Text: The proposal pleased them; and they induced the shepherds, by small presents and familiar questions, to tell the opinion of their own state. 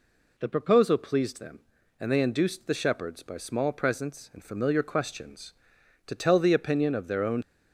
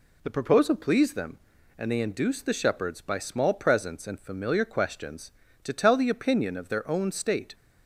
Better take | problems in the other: second | stops before "state"; at 7.4 s

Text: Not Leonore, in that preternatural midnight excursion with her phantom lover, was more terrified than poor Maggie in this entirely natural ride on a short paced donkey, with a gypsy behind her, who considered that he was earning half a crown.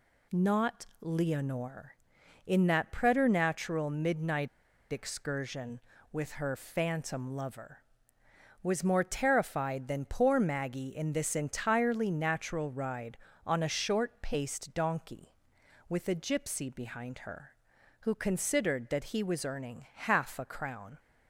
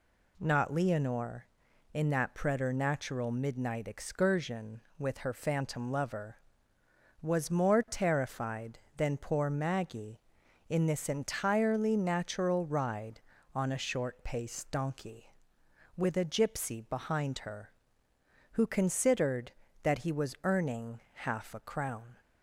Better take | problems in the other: second | pauses between "Not" and "Leonore"; slight; at 0.8 s; 0.16 s long // pauses between "midnight" and "excursion"; at 4.4 s; 0.45 s long

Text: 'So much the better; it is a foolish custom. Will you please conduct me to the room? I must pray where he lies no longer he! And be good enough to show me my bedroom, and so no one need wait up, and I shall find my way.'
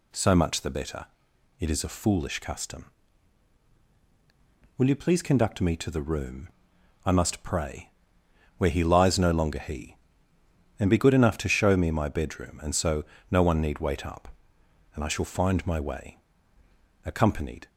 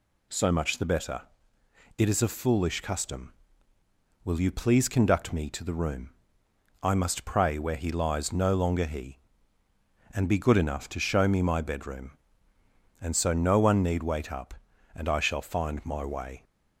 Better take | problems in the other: second | pauses between "pray" and "where"; noticeable; at 7.8 s; 0.70 s long // pauses between "so" and "no"; slight; at 13.0 s; 0.24 s long // goes on to say "Accompanied"; noticeable; from 17.0 s on; 0.62 s long

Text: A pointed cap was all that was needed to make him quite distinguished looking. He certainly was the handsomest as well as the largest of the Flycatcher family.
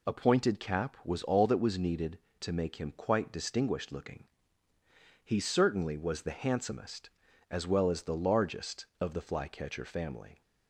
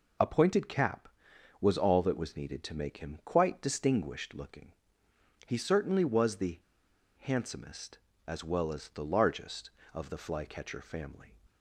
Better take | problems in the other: first | pauses between "the" and "handsomest"; noticeable; at 6.5 s; 0.60 s long

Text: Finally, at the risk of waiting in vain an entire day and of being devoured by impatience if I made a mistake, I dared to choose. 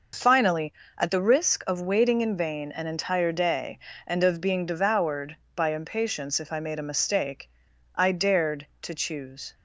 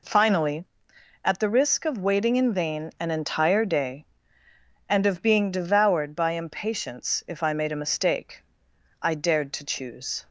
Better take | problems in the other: neither | none

